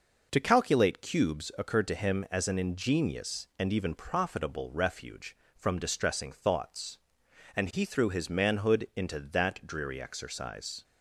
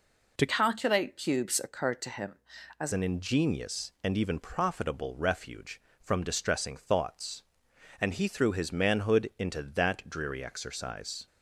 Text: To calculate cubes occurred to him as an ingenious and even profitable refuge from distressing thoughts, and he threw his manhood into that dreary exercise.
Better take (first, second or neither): first